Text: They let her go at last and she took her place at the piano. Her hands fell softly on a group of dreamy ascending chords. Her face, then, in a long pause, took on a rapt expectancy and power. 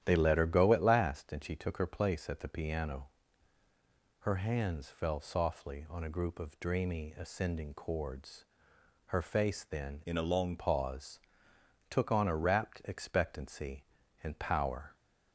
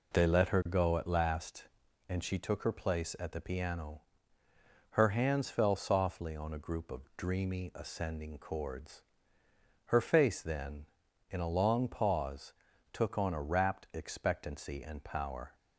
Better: second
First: starts louder than the rest; strong; until 1.0 s; 11 dB // changes voice from "in" to "long"; from 10.0 to 10.5 s; 0.5 s long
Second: none

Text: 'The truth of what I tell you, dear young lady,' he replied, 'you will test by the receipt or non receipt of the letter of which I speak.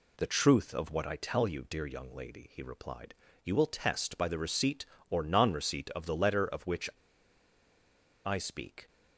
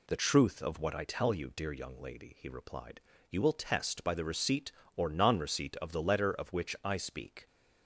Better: second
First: pauses between "which" and "I"; strong; at 6.8 s; 1.3 s long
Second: none

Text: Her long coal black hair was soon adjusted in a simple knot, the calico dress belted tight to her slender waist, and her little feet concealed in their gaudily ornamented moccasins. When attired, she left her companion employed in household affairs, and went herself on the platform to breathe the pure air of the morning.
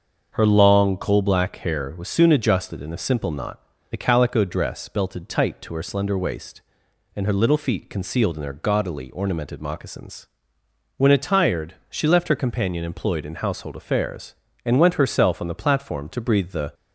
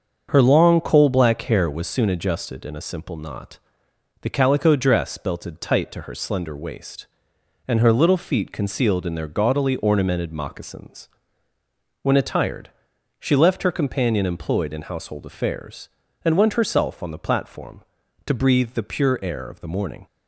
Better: second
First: starts louder than the rest; until 1.3 s; 6.5 dB // stops before "pure air of the morning"; at 16.7 s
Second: starts louder than the rest; until 1.3 s; 6.5 dB

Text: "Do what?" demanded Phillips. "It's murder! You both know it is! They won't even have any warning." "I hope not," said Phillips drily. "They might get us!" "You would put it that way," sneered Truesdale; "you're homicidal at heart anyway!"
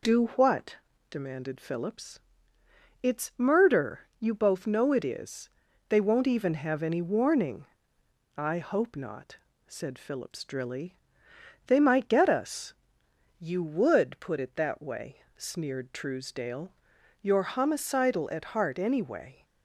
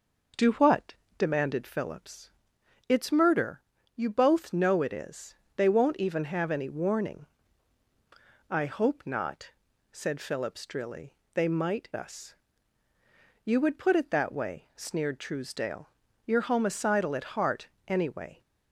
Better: first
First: none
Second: skips "get"; at 11.8 s // pauses between "heart" and "anyway"; slight; at 17.6 s; 0.18 s long

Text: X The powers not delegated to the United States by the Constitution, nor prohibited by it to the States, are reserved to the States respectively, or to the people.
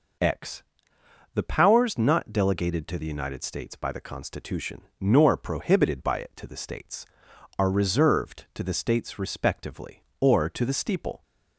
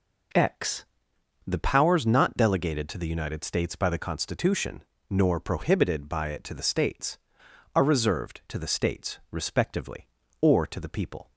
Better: second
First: pauses between "X" and "The"; noticeable; at 0.6 s; 0.72 s long // says "steeple" for "people"; at 10.7 s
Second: pauses between "X" and "The"; noticeable; at 0.8 s; 0.60 s long

